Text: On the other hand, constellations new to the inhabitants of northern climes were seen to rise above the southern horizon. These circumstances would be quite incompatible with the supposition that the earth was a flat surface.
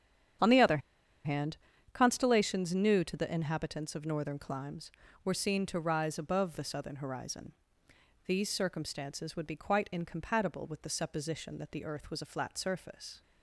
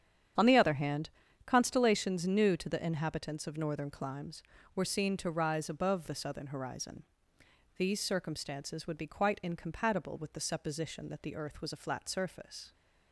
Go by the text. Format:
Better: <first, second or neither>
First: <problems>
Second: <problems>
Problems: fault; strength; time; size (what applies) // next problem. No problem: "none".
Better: second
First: starts louder than the rest; strong; until 2.2 s; 9 dB // pauses between "other" and "hand"; noticeable; at 0.7 s; 0.46 s long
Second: starts louder than the rest; strong; until 1.7 s; 8.5 dB